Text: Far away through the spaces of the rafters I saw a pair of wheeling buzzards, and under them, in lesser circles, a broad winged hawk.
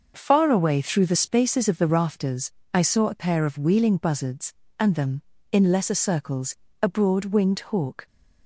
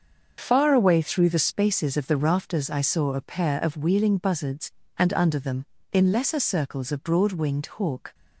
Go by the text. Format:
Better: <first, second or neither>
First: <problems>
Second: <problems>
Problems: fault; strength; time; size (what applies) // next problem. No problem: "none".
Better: second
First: starts louder than the rest; noticeable; until 1.1 s; 6 dB // pauses between "rafters" and "I"; slight; at 2.5 s; 0.24 s long // skips "under"; at 4.9 s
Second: starts louder than the rest; until 1.3 s; 6.5 dB